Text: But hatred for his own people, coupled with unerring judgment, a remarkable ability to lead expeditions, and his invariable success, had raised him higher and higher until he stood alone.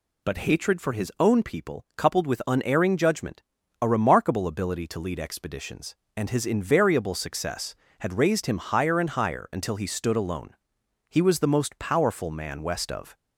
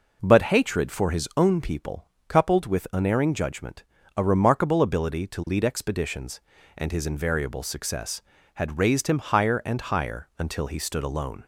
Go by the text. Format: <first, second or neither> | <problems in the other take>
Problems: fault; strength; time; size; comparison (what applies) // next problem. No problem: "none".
second | goes on to say "He was the most powerful man west of"; strong; from 11.1 s on; 2.0 s long